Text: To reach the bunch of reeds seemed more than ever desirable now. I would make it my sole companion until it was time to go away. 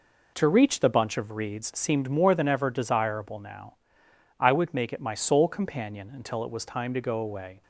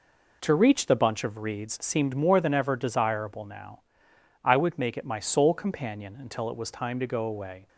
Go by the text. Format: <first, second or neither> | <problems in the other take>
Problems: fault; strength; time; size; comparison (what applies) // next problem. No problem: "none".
neither | none